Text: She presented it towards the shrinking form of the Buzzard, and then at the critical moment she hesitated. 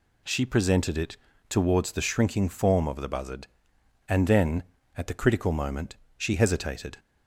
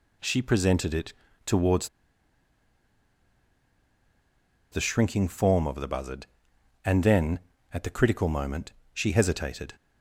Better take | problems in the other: first | pauses between "it" and "towards"; slight; at 1.1 s; 0.32 s long; slight in the first // pauses between "towards" and "the"; strong; at 1.8 s; 2.8 s long // pauses between "moment" and "she"; slight; at 8.7 s; 0.22 s long; slight in the first

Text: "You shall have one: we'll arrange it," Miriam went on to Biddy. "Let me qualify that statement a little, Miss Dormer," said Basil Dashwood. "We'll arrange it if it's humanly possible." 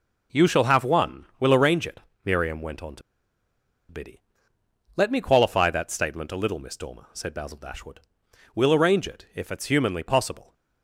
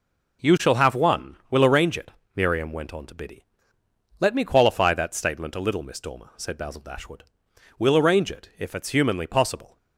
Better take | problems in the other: second | pauses between "to" and "Biddy"; noticeable; at 3.0 s; 0.89 s long

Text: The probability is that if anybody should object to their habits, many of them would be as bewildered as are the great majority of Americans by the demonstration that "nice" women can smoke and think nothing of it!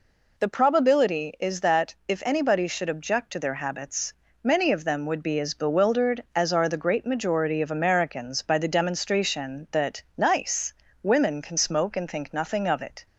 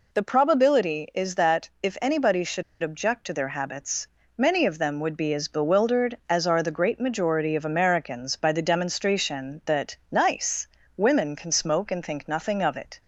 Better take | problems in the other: first | pauses between "should" and "object"; slight; at 2.6 s; 0.19 s long // pauses between "nice" and "women"; slight; at 10.6 s; 0.32 s long; slight in the first

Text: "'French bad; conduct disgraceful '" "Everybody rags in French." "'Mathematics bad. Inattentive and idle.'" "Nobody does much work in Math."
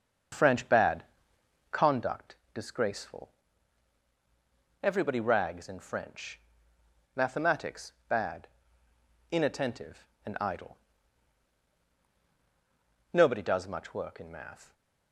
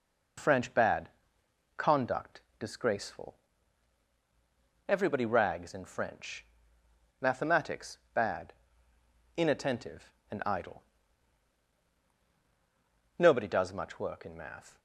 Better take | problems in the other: second | starts louder than the rest; until 2.1 s; 6 dB // pauses between "conduct" and "disgraceful"; slight; at 2.3 s; 0.18 s long; slight in the second // pauses between "Mathematics" and "bad"; slight; at 7.9 s; 0.16 s long; slight in the second

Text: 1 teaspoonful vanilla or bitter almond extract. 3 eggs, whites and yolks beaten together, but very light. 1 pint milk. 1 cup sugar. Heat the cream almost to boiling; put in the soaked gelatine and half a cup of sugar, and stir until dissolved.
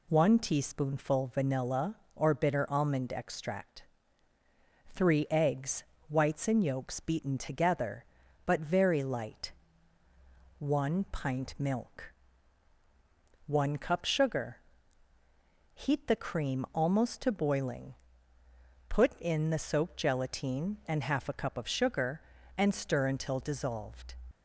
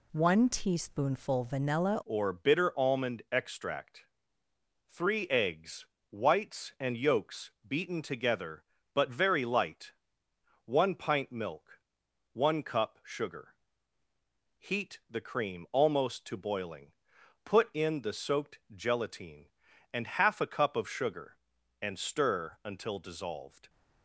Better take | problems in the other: first | changes voice at "or"; from 2.0 s on; 21.6 s long // pauses between "yolks" and "beaten"; slight; at 7.4 s; 0.18 s long // pauses between "soaked" and "gelatine"; slight; at 18.5 s; 0.16 s long

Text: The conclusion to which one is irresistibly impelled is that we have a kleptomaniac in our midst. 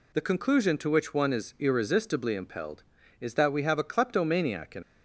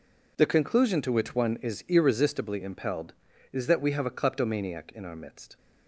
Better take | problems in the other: second | stops before "our midst"; at 4.8 s

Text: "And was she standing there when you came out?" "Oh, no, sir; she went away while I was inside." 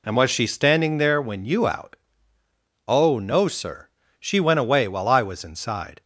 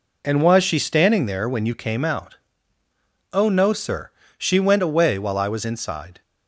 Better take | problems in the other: second | skips "came"; at 1.6 s

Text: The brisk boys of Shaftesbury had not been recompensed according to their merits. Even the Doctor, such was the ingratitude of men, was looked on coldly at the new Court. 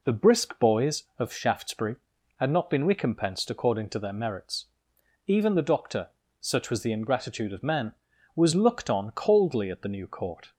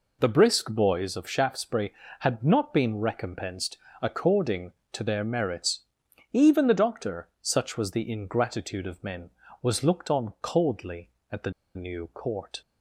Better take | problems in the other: first | pauses between "recompensed" and "according"; slight; at 3.7 s; 0.24 s long // pauses between "the" and "new"; slight; at 11.5 s; 0.24 s long

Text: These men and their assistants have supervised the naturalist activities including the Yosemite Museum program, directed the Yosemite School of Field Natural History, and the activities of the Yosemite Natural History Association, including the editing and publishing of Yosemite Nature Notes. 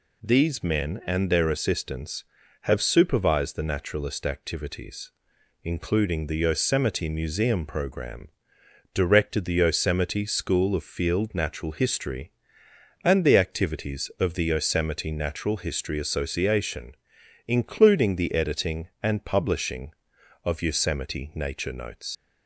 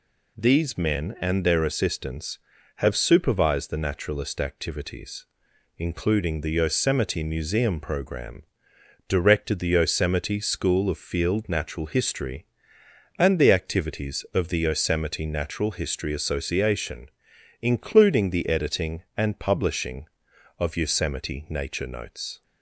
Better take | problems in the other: second | pauses between "activities" and "including"; noticeable; at 5.1 s; 0.52 s long; noticeable in the second // leaves "Notes" unfinished; at 22.1 s; 130 ms

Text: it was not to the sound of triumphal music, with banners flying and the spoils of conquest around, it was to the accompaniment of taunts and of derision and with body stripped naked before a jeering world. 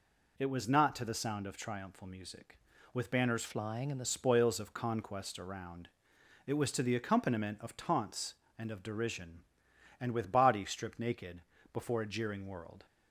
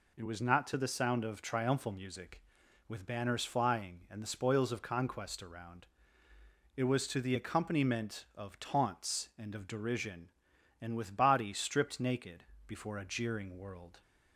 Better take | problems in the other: second | changes voice from "flying" to "the"; from 3.4 to 4.0 s; 0.6 s long // pauses between "naked" and "before"; slight; at 11.4 s; 0.32 s long; slight in the second

